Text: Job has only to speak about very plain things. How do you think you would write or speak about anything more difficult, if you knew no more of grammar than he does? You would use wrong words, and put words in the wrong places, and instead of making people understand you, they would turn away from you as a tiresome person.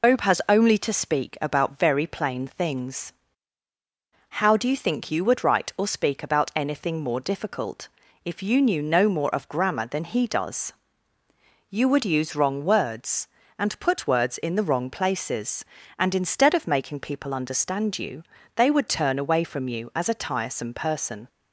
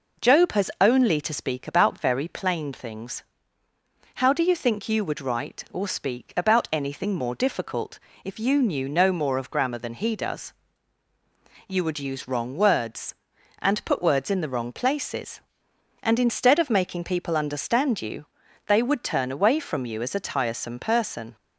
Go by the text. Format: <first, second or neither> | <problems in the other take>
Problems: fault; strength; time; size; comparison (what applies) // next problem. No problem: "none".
second | loses the start of "Job"; at 0.0 s; 115 ms